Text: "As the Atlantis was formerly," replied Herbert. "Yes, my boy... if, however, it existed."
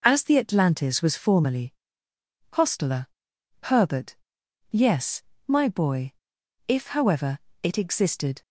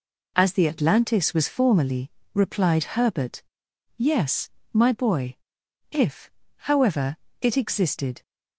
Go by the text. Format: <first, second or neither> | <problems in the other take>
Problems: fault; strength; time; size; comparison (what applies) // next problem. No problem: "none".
second | says "hostler" for "replied"; at 2.5 s